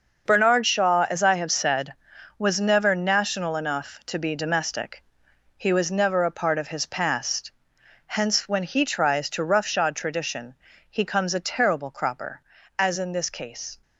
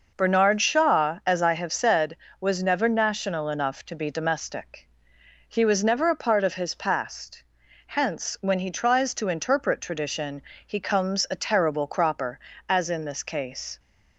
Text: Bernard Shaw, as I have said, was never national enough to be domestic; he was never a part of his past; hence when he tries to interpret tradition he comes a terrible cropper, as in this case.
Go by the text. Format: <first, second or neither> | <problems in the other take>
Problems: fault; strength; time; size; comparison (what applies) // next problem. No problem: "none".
second | starts louder than the rest; noticeable; until 1.2 s; 6 dB // says "roughshod" for "interpret"; at 9.4 s // pauses between "tradition" and "he"; slight; at 10.5 s; 0.36 s long; slight in the second